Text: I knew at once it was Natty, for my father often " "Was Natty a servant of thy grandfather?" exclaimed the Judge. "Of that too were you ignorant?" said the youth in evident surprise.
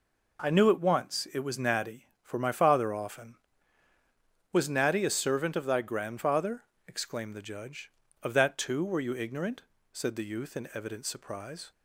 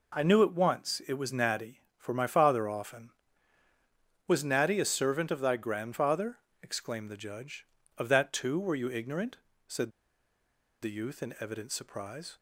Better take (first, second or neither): first